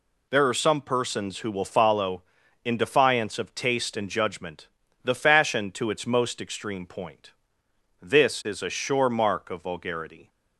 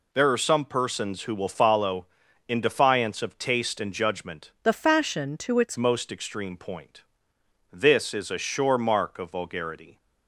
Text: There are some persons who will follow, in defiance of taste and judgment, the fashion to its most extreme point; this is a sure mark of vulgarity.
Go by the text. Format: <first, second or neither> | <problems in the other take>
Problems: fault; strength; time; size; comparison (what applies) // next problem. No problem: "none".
first | changes voice from "the" to "its"; from 4.6 to 5.7 s; 1.1 s long